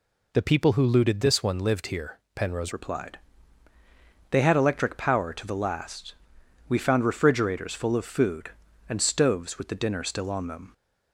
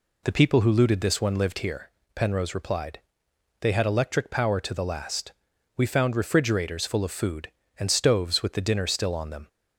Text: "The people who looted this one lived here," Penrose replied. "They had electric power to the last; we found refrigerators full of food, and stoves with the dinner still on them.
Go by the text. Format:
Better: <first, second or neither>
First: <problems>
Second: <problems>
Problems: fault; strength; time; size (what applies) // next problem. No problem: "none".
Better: second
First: changes voice at "replied"; from 2.7 s on; 8.0 s long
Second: none